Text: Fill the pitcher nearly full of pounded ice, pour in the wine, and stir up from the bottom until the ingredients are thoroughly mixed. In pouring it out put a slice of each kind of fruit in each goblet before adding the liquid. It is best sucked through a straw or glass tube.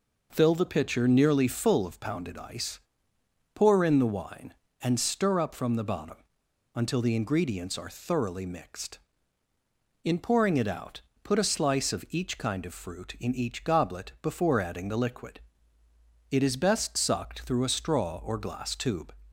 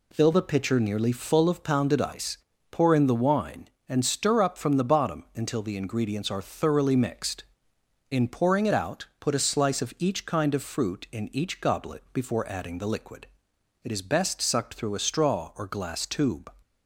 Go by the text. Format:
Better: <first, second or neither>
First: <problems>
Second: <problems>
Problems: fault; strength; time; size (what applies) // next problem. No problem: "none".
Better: second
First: pauses between "bottom" and "until"; noticeable; at 6.1 s; 0.59 s long // pauses between "out" and "put"; slight; at 11.0 s; 0.22 s long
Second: none